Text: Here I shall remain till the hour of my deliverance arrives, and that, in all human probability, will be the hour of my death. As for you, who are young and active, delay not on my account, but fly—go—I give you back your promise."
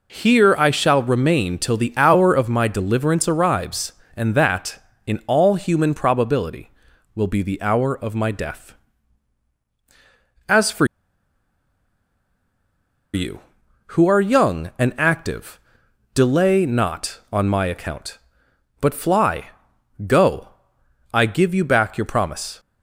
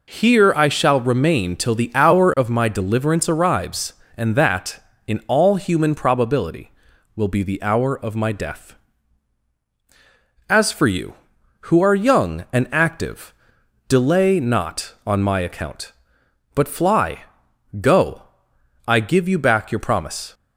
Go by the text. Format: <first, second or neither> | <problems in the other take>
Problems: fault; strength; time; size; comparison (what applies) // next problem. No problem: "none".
second | pauses between "for" and "you"; strong; at 10.8 s; 2.2 s long